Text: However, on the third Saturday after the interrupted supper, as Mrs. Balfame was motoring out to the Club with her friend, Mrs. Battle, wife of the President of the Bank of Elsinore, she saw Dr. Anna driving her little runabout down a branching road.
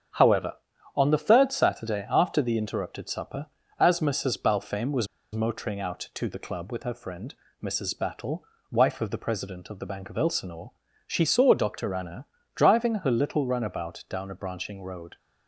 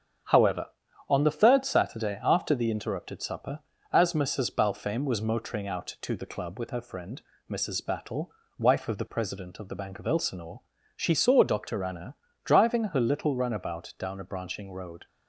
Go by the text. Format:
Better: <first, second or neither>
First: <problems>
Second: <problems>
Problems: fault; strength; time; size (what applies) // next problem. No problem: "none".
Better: second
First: starts louder than the rest; strong; until 1.5 s; 8.5 dB // pauses between "was" and "motoring"; slight; at 5.0 s; 0.26 s long // pauses between "Anna" and "driving"; slight; at 12.2 s; 0.30 s long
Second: starts louder than the rest; strong; until 1.7 s; 8.5 dB // pauses between "Anna" and "driving"; slight; at 12.1 s; 0.30 s long